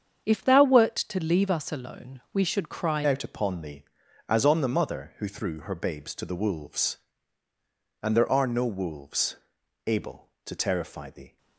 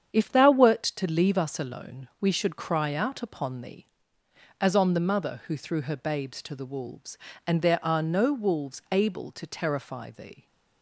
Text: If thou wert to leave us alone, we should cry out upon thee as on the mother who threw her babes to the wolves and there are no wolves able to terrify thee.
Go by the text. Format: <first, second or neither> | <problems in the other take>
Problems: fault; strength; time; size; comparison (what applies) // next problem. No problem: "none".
second | starts louder than the rest; strong; until 1.2 s; 7.5 dB; strong in the second // changes voice at "out"; from 3.0 s on; 8.3 s long // pauses between "wolves" and "able"; noticeable; at 9.3 s; 0.50 s long